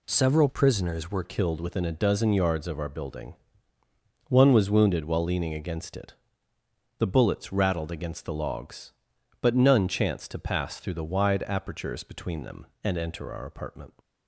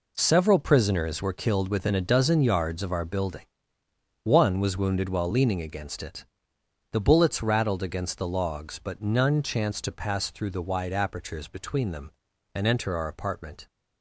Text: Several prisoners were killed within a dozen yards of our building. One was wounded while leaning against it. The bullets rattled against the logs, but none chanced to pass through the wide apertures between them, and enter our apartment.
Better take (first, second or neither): second